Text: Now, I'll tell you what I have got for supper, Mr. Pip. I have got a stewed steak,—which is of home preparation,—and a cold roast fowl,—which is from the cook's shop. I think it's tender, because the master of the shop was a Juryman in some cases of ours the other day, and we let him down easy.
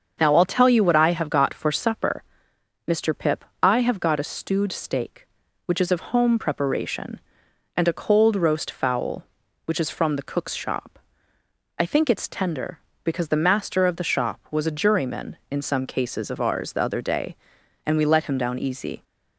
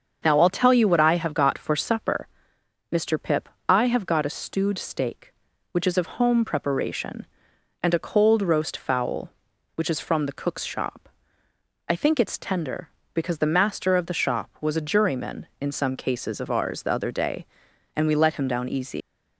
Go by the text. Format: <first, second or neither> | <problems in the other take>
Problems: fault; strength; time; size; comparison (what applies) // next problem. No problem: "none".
first | starts louder than the rest; until 1.2 s; 7 dB; also in the first // leaves "easy" unfinished; at 19.0 s; 125 ms